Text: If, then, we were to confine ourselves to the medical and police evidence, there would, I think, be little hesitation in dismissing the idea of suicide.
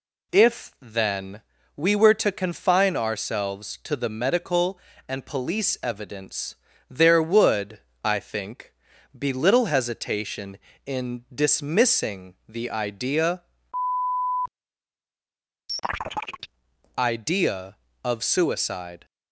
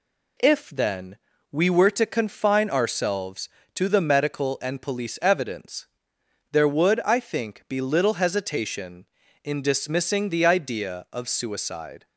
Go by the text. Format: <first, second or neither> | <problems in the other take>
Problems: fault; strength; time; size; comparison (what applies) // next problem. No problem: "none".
second | says "idea" twice; at 16.9 s